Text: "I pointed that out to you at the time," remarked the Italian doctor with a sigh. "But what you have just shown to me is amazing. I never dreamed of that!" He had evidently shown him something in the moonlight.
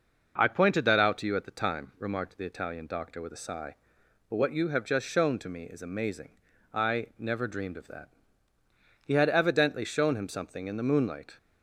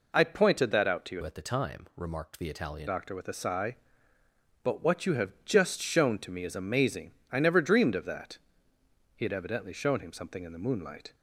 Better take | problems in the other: first | changes voice from "at" to "Italian"; from 1.2 to 2.8 s; 1.6 s long

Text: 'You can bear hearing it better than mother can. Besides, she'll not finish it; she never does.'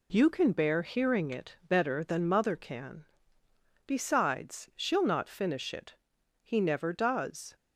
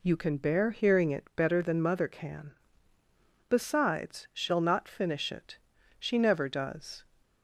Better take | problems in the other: second | says "he" for "she"; at 6.4 s

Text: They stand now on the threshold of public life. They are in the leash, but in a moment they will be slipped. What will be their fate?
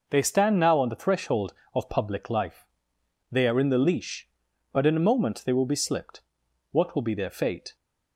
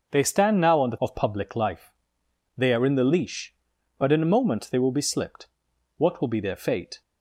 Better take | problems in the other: first | skips "threshold"; at 0.9 s

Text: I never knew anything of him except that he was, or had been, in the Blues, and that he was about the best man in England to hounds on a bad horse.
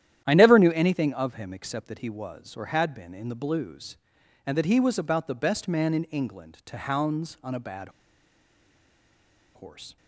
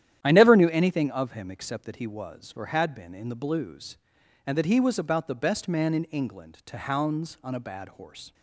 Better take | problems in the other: second | starts louder than the rest; strong; until 1.2 s; 11 dB; strong in the second // pauses between "bad" and "horse"; strong; at 7.8 s; 1.6 s long

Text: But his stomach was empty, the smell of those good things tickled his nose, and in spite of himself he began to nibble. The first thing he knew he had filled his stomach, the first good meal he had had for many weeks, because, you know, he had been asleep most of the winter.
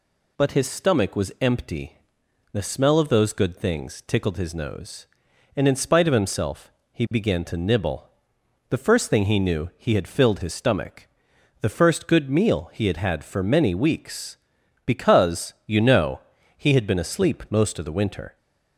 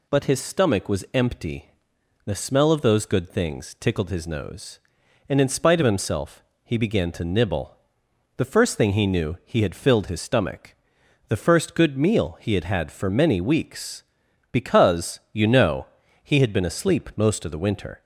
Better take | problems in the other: neither | pauses between "himself" and "he"; slight; the same in both

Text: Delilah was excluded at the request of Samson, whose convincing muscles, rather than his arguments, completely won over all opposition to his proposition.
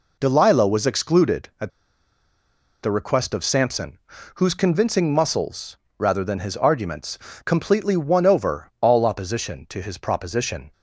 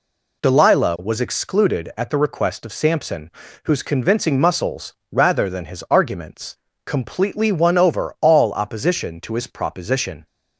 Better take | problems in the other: second | pauses between "at" and "the"; at 1.6 s; 1.1 s long

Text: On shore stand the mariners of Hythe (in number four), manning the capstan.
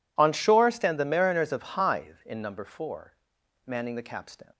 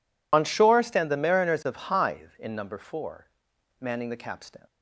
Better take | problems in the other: first | loses the start of "On"; at 0.3 s; 30 ms

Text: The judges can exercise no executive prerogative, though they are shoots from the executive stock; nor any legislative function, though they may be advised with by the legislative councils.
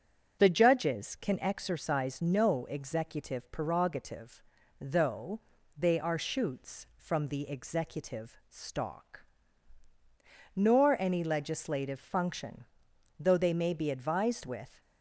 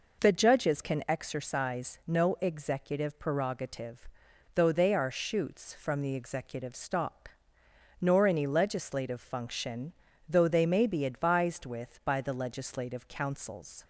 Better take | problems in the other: second | starts louder than the rest; until 1.4 s; 7 dB // pauses between "though" and "they"; at 5.3 s; 0.38 s long // stops before "by the legislative councils"; at 14.8 s

